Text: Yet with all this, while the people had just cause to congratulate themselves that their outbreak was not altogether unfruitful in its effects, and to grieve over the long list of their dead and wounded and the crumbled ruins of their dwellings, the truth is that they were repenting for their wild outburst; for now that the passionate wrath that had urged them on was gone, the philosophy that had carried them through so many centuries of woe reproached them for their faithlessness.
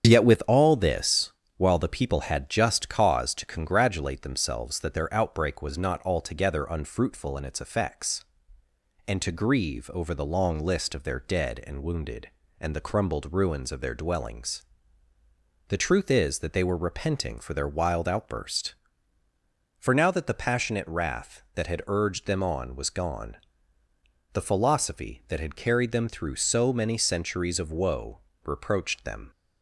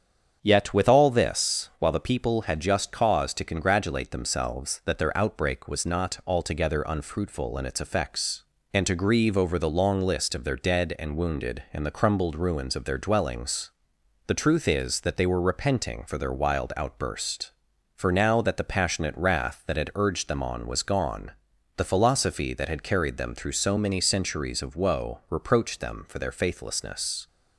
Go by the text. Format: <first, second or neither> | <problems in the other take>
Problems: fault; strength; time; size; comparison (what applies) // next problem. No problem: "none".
second | starts louder than the rest; strong; until 1.0 s; 8 dB; strong in the second // pauses between "woe" and "reproached"; slight; at 28.2 s; 0.24 s long // stops before "for their faithlessness"; at 29.3 s